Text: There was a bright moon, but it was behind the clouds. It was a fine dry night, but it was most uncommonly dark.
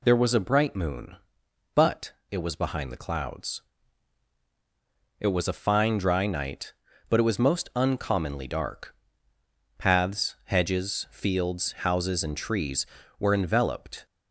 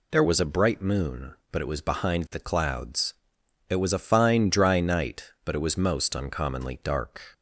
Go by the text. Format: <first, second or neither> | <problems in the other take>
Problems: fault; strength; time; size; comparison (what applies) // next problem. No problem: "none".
second | pauses between "but" and "it"; slight; at 2.1 s; 0.18 s long // goes on to say "Paths hedges fields houses and trees were enveloped"; strong; from 9.7 s on; 4.2 s long